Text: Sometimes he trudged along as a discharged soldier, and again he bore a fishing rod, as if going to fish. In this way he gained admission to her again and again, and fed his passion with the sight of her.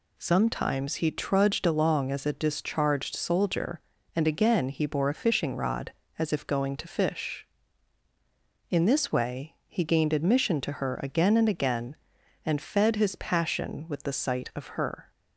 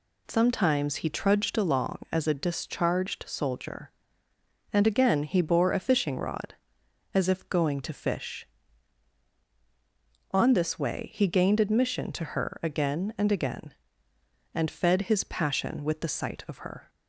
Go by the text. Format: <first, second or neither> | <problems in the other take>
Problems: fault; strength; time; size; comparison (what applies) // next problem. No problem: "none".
first | says "On" for "In"; at 10.3 s